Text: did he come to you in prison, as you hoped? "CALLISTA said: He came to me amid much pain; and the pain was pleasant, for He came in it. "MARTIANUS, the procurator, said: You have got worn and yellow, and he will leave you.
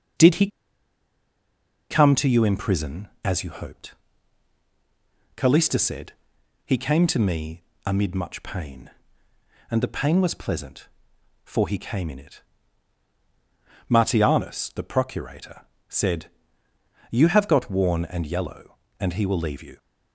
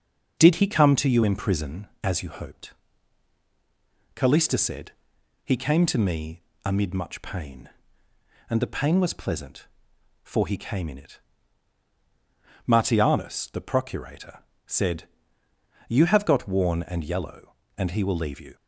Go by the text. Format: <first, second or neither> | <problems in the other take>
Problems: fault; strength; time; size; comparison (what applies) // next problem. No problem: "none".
second | starts louder than the rest; noticeable; until 2.6 s; 6 dB; noticeable in the second // pauses between "he" and "come"; strong; at 0.4 s; 1.4 s long // pauses between "me" and "amid"; slight; at 7.6 s; 0.20 s long; slight in the second